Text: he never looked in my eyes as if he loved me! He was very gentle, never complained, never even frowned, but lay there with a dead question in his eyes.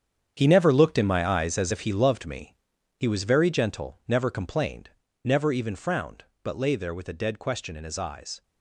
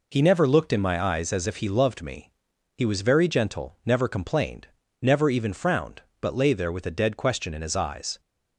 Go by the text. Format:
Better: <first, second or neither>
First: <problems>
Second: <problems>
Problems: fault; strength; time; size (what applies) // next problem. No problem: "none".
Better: second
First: gets quieter; strong; throughout; 12.5 dB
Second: none